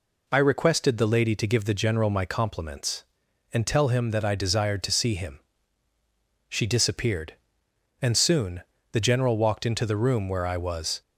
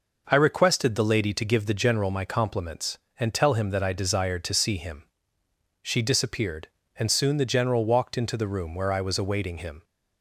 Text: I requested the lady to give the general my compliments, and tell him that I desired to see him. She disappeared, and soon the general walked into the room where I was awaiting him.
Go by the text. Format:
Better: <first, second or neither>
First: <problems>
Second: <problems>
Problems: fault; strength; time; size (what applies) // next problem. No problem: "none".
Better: second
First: pauses between "soon" and "the"; slight; at 8.6 s; 0.28 s long // stops before "awaiting him"; at 11.0 s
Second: none